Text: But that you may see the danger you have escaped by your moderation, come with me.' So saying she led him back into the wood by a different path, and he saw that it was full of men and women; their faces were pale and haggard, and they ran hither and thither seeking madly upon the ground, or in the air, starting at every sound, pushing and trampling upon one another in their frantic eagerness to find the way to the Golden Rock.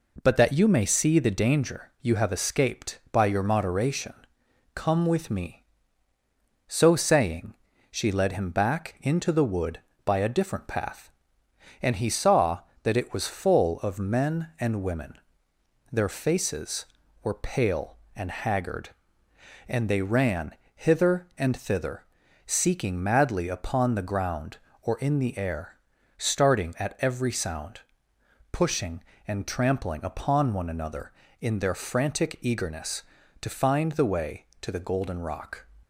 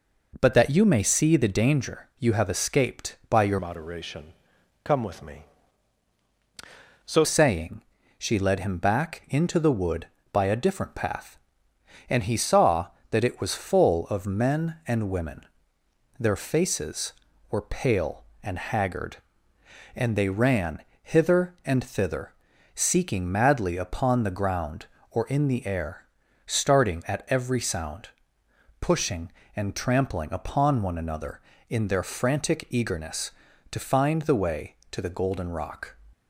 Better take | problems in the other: first | changes voice from "moderation" to "So"; from 3.5 to 7.2 s; 3.7 s long // pauses between "saying" and "she"; slight; at 7.8 s; 0.36 s long; slight in the first // pauses between "ran" and "hither"; slight; at 20.8 s; 0.20 s long; slight in the first // pauses between "thither" and "seeking"; noticeable; at 22.3 s; 0.46 s long; noticeable in the first

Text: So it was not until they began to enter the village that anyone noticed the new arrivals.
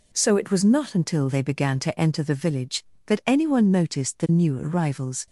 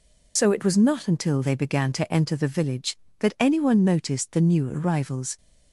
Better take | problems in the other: first | loses the start of "So"; at 0.3 s; 65 ms

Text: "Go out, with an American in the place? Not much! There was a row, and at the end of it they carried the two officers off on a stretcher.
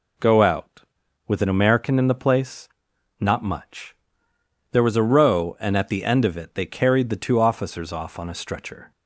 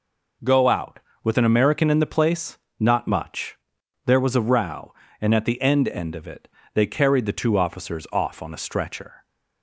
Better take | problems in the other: first | says "end" twice; at 5.8 s // pauses between "it" and "they"; slight; at 6.4 s; 0.24 s long

